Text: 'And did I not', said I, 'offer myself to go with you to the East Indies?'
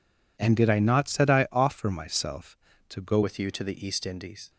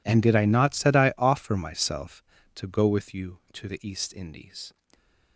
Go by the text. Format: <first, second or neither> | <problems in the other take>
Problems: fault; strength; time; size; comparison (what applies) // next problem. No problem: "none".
second | changes voice at "with"; from 3.2 s on; 1.3 s long